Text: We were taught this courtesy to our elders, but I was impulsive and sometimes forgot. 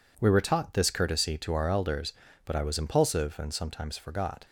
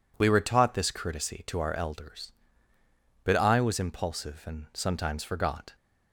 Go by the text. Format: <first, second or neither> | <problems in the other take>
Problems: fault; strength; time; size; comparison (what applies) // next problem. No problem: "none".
neither | none